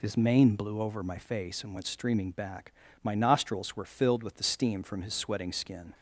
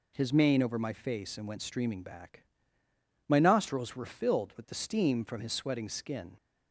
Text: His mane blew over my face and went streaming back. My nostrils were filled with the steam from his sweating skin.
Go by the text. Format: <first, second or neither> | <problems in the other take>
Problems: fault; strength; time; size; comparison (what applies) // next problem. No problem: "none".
first | skips "blew"; at 0.6 s